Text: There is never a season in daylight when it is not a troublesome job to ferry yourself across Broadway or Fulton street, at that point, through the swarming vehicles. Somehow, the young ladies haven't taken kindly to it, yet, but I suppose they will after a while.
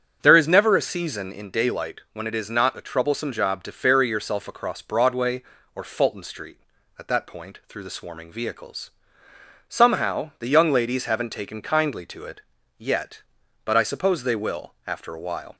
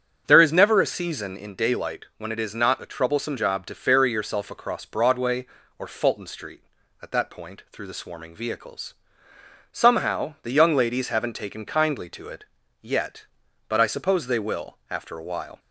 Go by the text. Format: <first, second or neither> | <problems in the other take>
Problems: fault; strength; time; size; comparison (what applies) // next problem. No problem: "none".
neither | starts louder than the rest; the same in both